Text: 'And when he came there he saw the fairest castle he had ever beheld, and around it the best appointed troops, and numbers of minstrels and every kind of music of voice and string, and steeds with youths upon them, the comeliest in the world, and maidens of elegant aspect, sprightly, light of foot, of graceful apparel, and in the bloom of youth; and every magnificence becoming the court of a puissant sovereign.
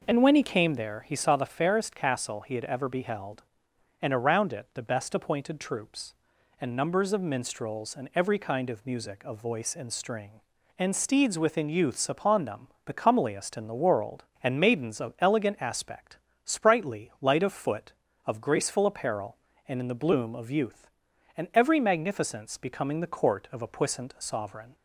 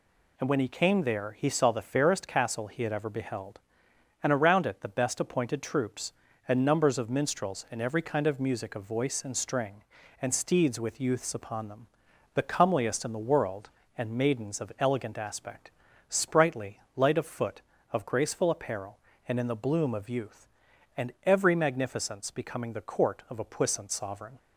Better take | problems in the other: second | says "within" for "with"; at 11.3 s

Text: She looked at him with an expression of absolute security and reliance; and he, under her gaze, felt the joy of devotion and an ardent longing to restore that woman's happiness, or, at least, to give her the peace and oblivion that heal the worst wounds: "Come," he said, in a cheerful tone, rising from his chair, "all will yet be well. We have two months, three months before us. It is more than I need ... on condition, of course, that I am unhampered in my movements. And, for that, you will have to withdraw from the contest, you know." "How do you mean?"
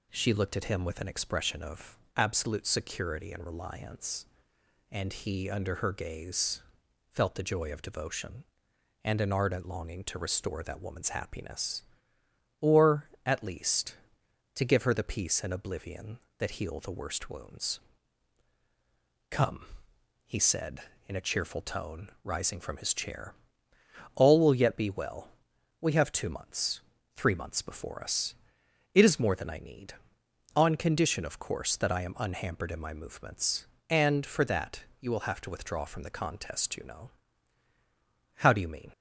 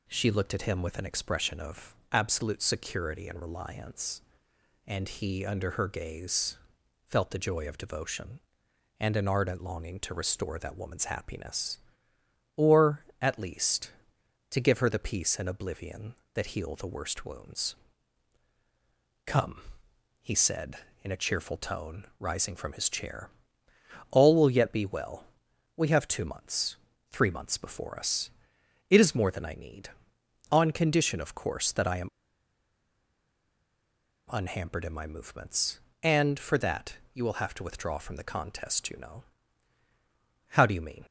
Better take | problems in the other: first | pauses between "of" and "absolute"; slight; at 1.9 s; 0.16 s long; slight in the first // pauses between "am" and "unhampered"; strong; at 32.0 s; 2.2 s long

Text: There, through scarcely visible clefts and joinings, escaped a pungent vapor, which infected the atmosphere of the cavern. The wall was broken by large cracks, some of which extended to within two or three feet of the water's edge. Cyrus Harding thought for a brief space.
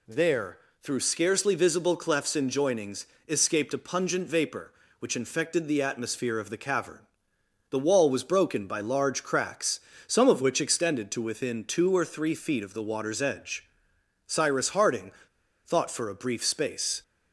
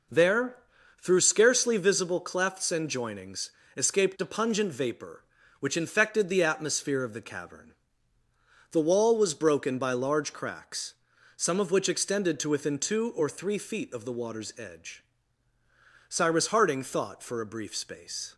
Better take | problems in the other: second | pauses between "Harding" and "thought"; noticeable; at 15.1 s; 0.53 s long

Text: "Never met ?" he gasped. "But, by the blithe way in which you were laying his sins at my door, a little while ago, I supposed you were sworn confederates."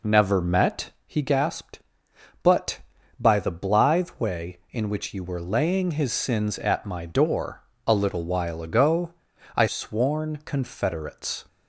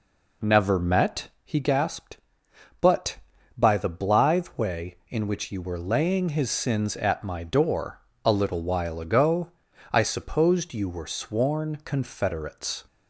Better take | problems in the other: second | skips "supposed you were"; at 9.6 s

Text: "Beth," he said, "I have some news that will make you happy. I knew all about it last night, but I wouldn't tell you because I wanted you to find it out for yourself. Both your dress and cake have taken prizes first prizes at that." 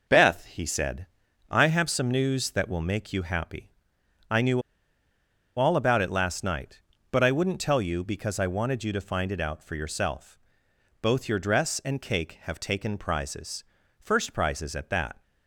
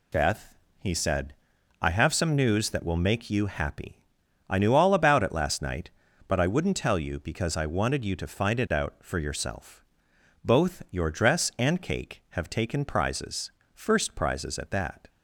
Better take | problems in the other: second | pauses between "knew" and "all"; noticeable; at 4.6 s; 0.95 s long // pauses between "prizes" and "first"; slight; at 13.6 s; 0.34 s long; slight in the second

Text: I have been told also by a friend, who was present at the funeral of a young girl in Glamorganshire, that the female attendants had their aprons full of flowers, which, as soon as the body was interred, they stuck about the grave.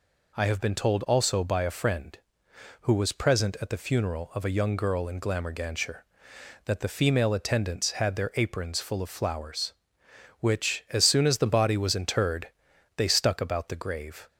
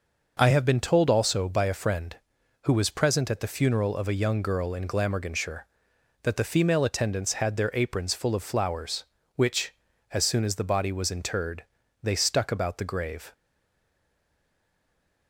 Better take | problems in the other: first | stays silent after the last word; noticeable; from 13.3 s on; 1.9 s long

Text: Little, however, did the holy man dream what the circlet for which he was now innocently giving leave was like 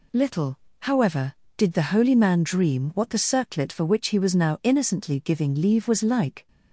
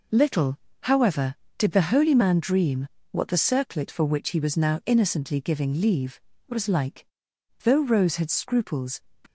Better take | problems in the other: first | pauses between "dream" and "what"; slight; at 2.8 s; 0.24 s long // goes on to say "Though Rose had scruples"; from 7.6 s on; 1.4 s long

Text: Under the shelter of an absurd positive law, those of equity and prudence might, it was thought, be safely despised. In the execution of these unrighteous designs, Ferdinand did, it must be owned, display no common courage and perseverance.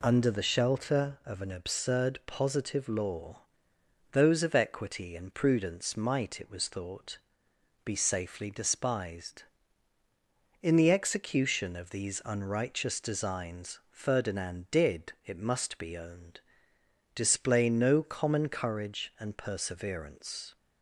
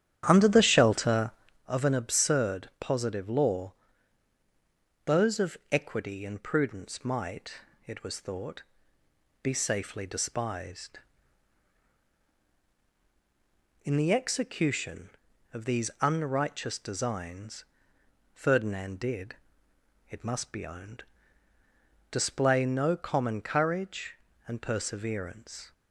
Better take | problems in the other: first | starts louder than the rest; strong; until 1.6 s; 10 dB

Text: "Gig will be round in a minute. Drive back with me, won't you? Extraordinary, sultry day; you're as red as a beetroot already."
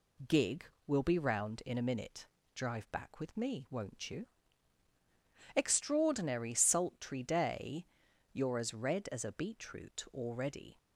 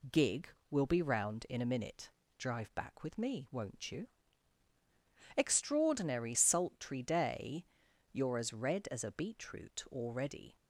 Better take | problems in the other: neither | none

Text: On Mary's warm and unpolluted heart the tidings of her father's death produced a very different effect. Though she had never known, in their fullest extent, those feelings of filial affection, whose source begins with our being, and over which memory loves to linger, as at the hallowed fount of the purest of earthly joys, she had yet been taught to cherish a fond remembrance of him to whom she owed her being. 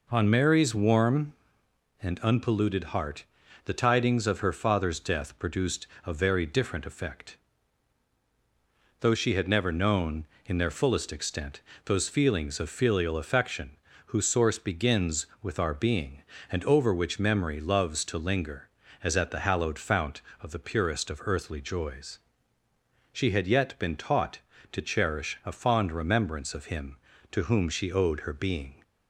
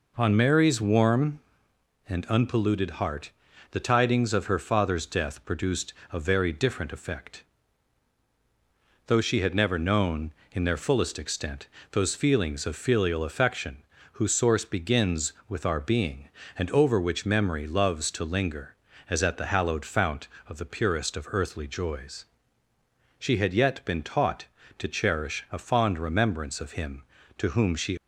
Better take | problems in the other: first | pauses between "heart" and "the"; at 3.3 s; 0.40 s long; also in the first // pauses between "produced" and "a"; slight; at 5.9 s; 0.20 s long; slight in the first // stops before "owed her being"; at 27.9 s

